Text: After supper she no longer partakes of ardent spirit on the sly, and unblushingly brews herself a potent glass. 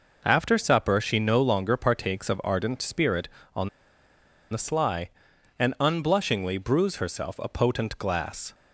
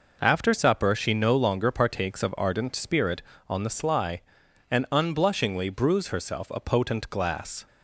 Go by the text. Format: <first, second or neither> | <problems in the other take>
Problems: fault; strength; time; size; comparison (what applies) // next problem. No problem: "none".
second | pauses between "on" and "the"; noticeable; at 3.6 s; 0.83 s long